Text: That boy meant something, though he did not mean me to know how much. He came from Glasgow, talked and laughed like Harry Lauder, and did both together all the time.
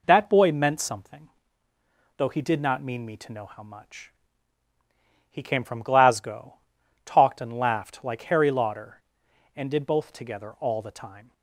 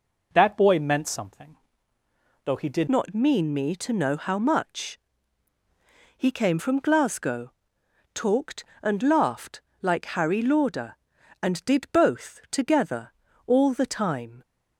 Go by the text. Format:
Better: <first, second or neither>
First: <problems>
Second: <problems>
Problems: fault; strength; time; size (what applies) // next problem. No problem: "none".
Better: first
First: none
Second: changes voice at "not"; from 2.8 s on; 11.6 s long // pauses between "laughed" and "like"; slight; at 9.6 s; 0.20 s long // pauses between "together" and "all"; slight; at 13.1 s; 0.34 s long